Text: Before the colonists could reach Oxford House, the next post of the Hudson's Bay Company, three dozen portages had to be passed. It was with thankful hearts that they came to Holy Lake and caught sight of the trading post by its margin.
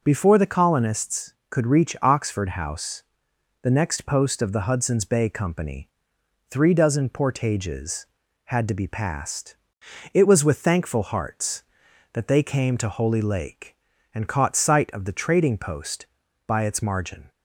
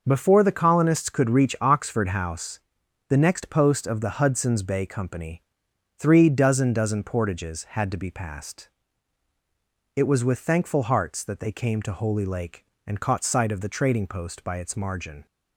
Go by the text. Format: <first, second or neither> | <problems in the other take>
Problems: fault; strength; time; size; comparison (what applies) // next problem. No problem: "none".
first | says "dozen" twice; at 6.7 s